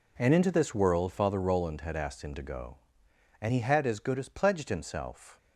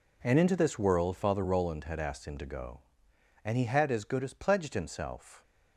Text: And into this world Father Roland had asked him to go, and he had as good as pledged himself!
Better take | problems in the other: neither | none

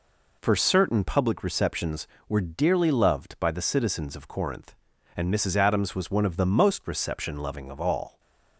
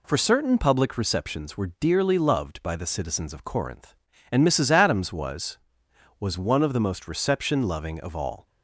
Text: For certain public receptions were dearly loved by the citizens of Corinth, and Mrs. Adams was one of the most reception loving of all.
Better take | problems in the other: first | says "was" twice; at 6.1 s

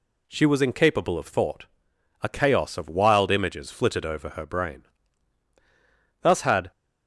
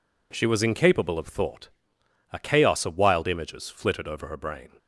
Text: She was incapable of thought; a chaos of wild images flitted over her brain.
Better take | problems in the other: second | goes on to say "Thus had"; slight; from 6.2 s on; 0.48 s long

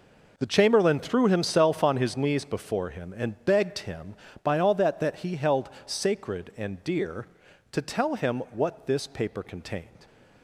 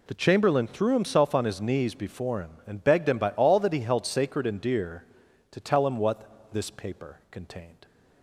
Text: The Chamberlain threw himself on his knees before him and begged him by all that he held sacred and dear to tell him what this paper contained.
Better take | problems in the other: second | says "that" twice; at 4.9 s // pauses between "held" and "sacred"; slight; at 5.6 s; 0.16 s long

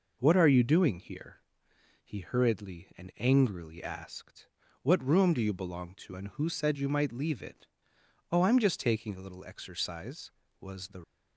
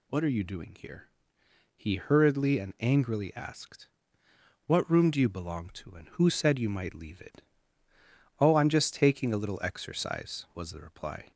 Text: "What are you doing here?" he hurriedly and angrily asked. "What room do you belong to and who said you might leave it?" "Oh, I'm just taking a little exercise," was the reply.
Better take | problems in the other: second | stops before "reply"; at 11.0 s

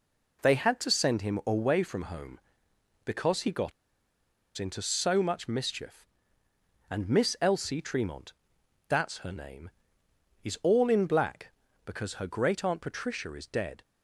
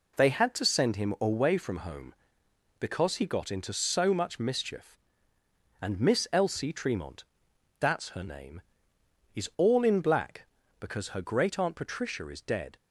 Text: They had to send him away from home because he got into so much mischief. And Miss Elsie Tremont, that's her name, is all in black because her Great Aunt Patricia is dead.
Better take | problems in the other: second | pauses between "got" and "into"; noticeable; at 3.7 s; 0.86 s long

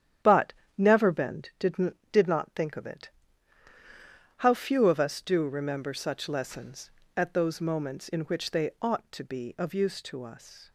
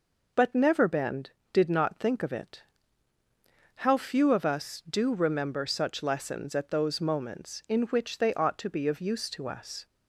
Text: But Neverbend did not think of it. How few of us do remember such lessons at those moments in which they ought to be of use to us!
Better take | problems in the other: second | starts louder than the rest; strong; until 1.4 s; 10 dB // pauses between "But" and "Neverbend"; slight; at 0.5 s; 0.24 s long // says "did" twice; at 2.1 s

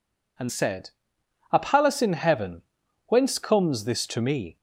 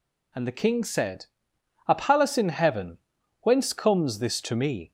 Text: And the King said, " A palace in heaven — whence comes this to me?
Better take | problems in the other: second | skips "the King"; at 0.4 s

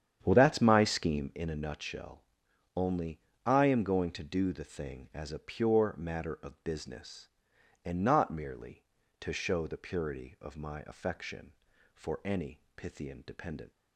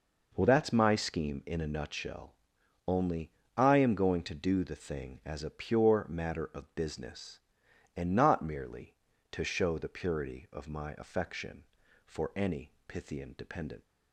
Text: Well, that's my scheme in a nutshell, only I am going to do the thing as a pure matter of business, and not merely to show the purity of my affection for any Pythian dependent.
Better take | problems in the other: second | starts louder than the rest; strong; until 1.4 s; 9 dB // pauses between "only" and "I"; slight; at 3.1 s; 0.26 s long; slight in the second // pauses between "any" and "Pythian"; slight; at 12.5 s; 0.16 s long; slight in the second

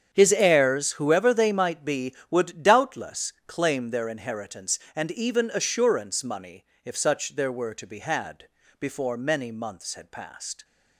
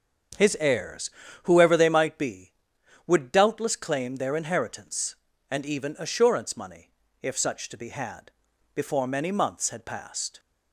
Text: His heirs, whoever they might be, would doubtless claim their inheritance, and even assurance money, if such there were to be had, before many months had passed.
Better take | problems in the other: first | starts louder than the rest; strong; until 1.7 s; 7.5 dB; strong in the first // skips "there were"; at 7.6 s

